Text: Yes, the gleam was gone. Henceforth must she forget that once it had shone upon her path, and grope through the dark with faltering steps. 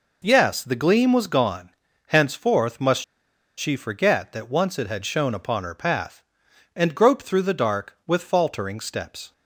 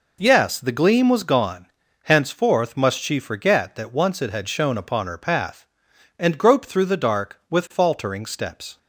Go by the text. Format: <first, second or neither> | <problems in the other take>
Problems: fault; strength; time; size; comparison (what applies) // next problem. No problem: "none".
second | pauses between "must" and "she"; noticeable; at 3.0 s; 0.54 s long